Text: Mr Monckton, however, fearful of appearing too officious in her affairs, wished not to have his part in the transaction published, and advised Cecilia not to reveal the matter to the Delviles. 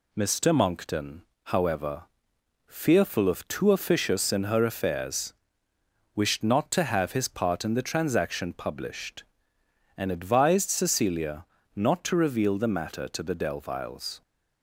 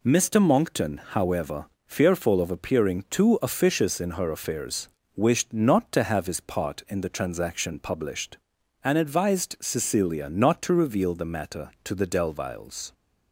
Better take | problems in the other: second | skips "appearing"; at 3.4 s // pauses between "Cecilia" and "not"; slight; at 11.4 s; 0.32 s long

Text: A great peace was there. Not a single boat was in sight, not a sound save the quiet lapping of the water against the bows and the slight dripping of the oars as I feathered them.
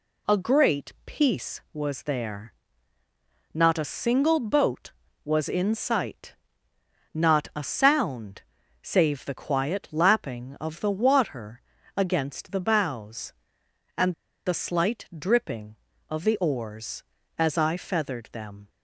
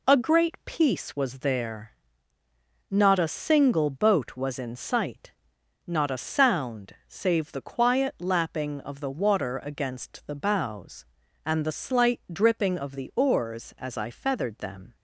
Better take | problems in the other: second | pauses between "sound" and "save"; at 8.4 s; 0.40 s long // pauses between "water" and "against"; slight; at 11.6 s; 0.34 s long // pauses between "and" and "the"; slight; at 14.1 s; 0.32 s long

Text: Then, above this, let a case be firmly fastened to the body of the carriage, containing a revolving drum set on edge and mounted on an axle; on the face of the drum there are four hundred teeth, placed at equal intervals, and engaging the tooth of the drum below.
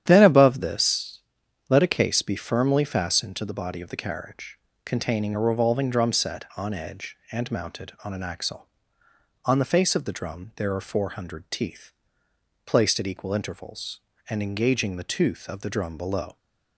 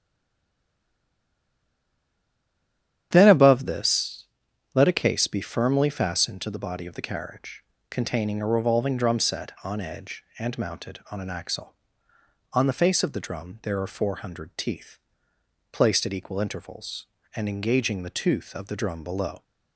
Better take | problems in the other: first | stays silent before the first word; strong; until 3.1 s; 3.1 s long // starts louder than the rest; strong; until 4.1 s; 10 dB; strong in the first

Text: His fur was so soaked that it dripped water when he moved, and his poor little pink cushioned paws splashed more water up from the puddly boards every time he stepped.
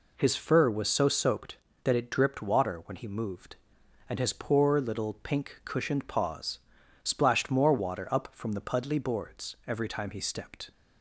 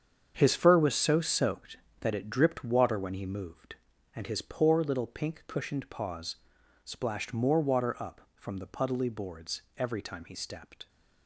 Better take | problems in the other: first | gets quieter; strong; throughout; 11.5 dB // pauses between "paws" and "splashed"; noticeable; at 6.3 s; 0.48 s long; also in the first // pauses between "boards" and "every"; slight; at 9.6 s; 0.16 s long

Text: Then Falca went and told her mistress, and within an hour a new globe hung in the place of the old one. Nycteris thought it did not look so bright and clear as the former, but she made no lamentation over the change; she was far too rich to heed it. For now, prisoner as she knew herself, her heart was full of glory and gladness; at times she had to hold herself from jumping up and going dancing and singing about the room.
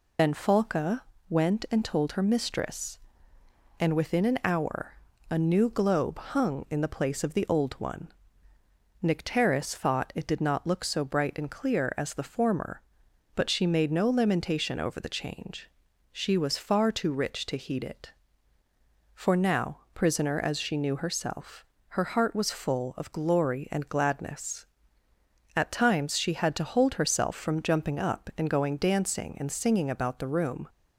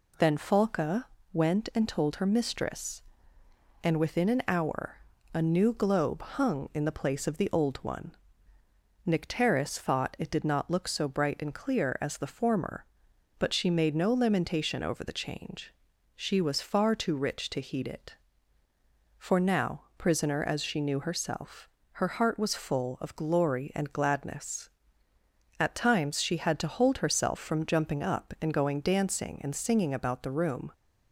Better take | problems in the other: second | loses the start of "Then"; at 0.1 s; 95 ms // pauses between "Falca" and "went"; slight; at 1.0 s; 0.26 s long; slight in the second // pauses between "hour" and "a"; slight; at 4.9 s; 0.34 s long; slight in the second

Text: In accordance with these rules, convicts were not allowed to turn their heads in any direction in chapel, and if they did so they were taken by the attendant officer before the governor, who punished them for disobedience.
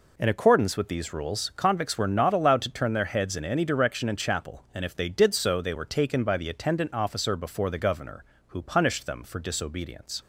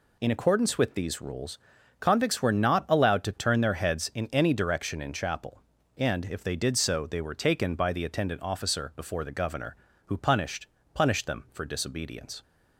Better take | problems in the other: first | says "punished" twice; at 10.9 s

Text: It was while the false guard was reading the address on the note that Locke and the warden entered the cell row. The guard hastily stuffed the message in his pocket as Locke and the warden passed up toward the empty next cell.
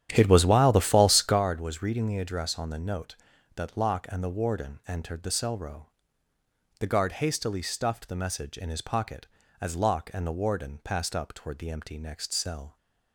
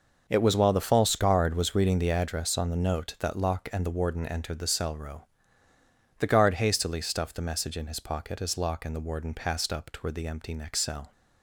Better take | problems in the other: second | starts louder than the rest; strong; until 1.4 s; 10 dB

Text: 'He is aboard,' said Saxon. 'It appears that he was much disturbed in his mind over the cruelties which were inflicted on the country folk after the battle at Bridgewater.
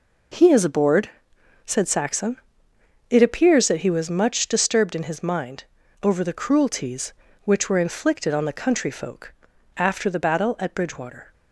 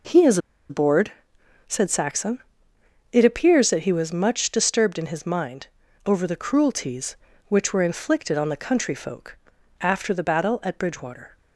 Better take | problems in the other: first | pauses between "is" and "aboard"; slight; at 0.3 s; 0.31 s long // pauses between "mind" and "over"; at 5.6 s; 0.38 s long; also in the first // pauses between "folk" and "after"; at 9.3 s; 0.42 s long; also in the first

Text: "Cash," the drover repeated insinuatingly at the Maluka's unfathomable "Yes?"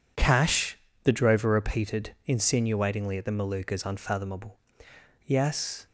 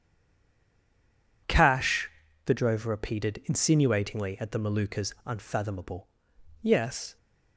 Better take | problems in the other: first | stays silent before the first word; noticeable; until 1.4 s; 1.4 s long // pauses between "unfathomable" and "Yes"; noticeable; at 6.0 s; 0.56 s long; noticeable in the first

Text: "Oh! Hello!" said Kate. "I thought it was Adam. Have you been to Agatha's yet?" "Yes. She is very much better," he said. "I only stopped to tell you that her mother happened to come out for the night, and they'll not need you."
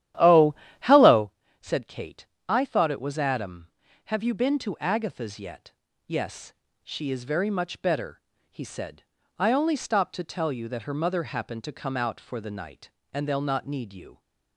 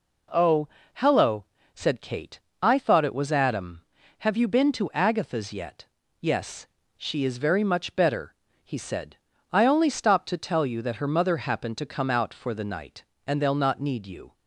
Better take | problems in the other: second | starts louder than the rest; strong; until 1.3 s; 11.5 dB

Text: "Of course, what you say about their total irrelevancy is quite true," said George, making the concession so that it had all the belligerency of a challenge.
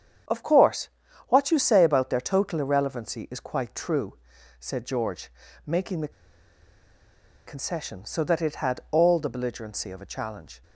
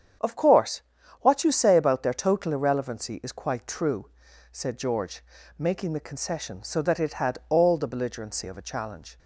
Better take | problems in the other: second | starts louder than the rest; strong; until 1.7 s; 8 dB; strong in the second // pauses between "the" and "concession"; strong; at 6.1 s; 1.3 s long

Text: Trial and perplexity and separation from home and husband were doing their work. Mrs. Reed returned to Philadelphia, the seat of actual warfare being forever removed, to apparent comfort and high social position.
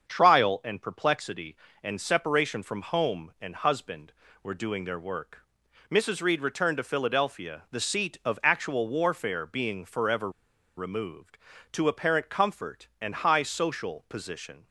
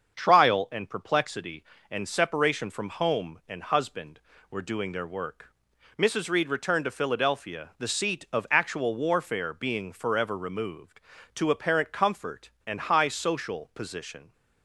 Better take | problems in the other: second | starts louder than the rest; until 1.1 s; 7 dB; also in the second // pauses between "forever" and "removed"; noticeable; at 10.2 s; 0.47 s long

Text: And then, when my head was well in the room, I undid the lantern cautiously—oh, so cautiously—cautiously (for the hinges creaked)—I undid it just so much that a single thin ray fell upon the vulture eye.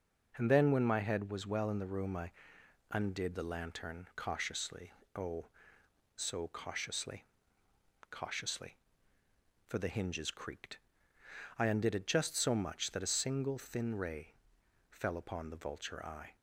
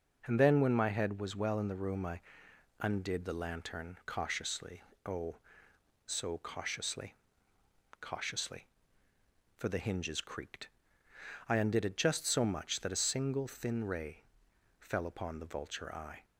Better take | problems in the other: neither | pauses between "I" and "undid"; noticeable; the same in both // pauses between "ray" and "fell"; noticeable; the same in both

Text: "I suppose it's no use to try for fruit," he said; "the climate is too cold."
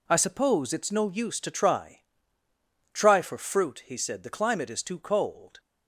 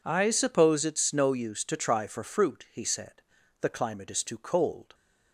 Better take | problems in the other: second | says "try" twice; at 2.9 s

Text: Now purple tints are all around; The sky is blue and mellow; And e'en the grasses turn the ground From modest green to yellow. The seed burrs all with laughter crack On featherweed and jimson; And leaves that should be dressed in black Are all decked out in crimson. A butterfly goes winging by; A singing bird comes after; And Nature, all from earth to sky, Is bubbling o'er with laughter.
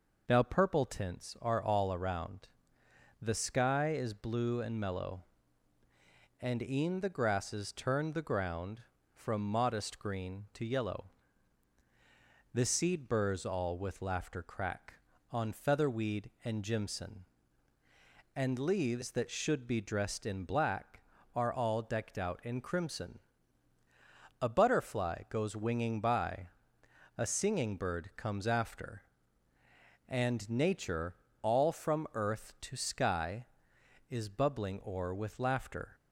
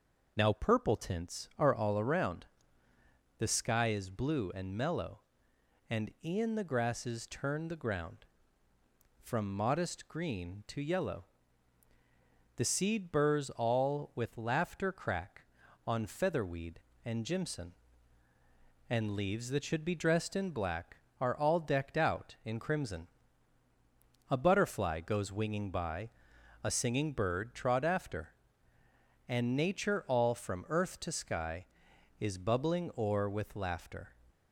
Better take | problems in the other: first | says "trod" for "comes"; at 27.5 s

